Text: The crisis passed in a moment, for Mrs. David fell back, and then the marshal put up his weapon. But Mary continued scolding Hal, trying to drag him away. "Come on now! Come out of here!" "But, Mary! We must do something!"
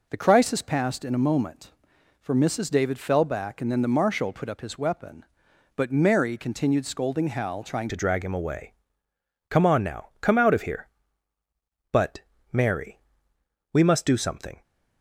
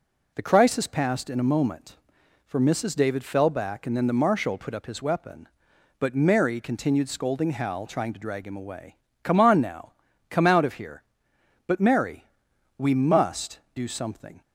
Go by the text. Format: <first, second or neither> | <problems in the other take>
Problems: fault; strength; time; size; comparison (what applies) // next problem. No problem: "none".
second | changes voice at "to"; from 7.8 s on; 6.8 s long